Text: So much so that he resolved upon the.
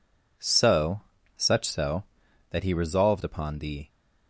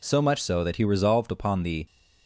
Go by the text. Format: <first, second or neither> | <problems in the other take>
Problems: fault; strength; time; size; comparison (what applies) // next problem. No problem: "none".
second | says "such" for "much"; at 1.3 s